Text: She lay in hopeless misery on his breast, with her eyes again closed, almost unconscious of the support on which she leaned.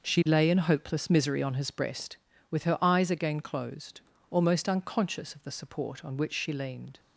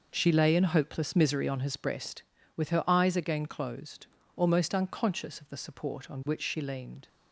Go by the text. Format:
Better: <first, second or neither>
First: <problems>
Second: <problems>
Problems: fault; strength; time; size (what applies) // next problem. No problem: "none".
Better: neither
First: none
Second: none